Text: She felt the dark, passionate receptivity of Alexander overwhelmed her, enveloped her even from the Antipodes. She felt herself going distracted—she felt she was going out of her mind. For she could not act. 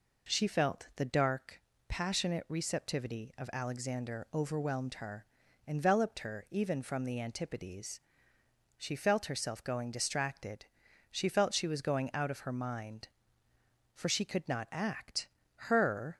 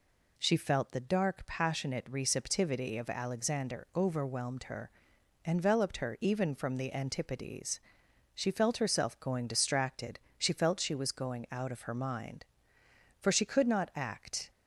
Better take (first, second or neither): second